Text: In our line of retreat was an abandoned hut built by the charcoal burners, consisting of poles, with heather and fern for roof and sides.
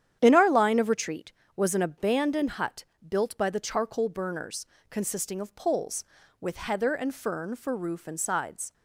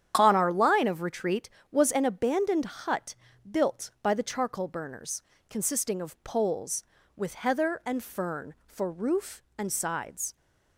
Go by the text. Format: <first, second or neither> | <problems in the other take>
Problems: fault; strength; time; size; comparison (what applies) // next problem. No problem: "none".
first | starts louder than the rest; strong; until 1.1 s; 9.5 dB; strong in the first // says "On" for "In"; at 0.1 s // pauses between "hut" and "built"; slight; at 3.1 s; 0.34 s long; slight in the first